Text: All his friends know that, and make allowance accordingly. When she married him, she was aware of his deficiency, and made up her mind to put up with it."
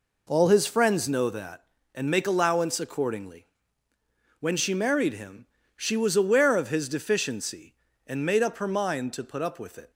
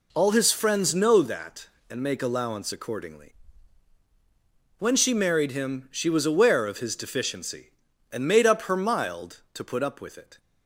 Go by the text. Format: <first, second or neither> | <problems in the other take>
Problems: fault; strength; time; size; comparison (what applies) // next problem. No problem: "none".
first | says "mild" for "mind"; at 8.7 s